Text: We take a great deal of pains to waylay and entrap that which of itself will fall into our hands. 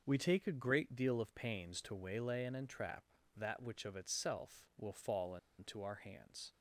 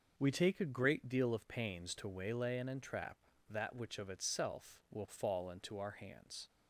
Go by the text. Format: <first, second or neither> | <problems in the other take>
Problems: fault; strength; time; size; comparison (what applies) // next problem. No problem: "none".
second | pauses between "fall" and "into"; slight; at 5.3 s; 0.25 s long